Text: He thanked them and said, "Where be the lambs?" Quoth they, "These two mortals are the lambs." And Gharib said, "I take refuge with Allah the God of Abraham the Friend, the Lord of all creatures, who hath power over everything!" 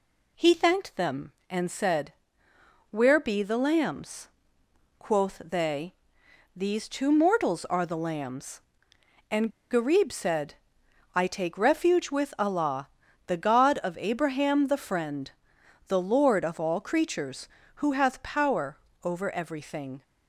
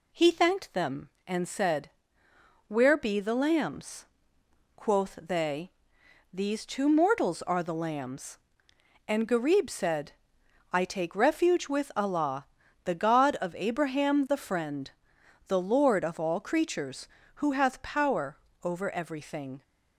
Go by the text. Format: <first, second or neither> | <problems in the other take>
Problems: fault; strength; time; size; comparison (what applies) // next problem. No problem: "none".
second | pauses between "And" and "Gharib"; slight; at 9.4 s; 0.21 s long // pauses between "Allah" and "the"; at 12.8 s; 0.38 s long; also in the second // pauses between "power" and "over"; slight; at 18.7 s; 0.24 s long; slight in the second